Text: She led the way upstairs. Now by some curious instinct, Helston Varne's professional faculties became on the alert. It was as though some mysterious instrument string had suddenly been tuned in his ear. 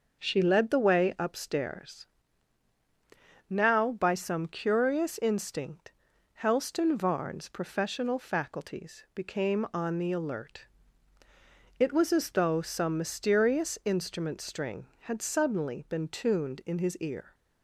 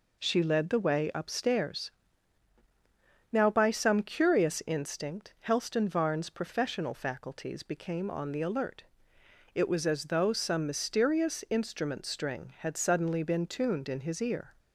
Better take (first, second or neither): neither